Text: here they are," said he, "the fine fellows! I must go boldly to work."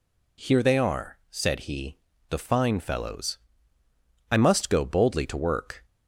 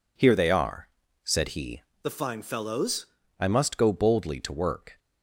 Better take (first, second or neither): first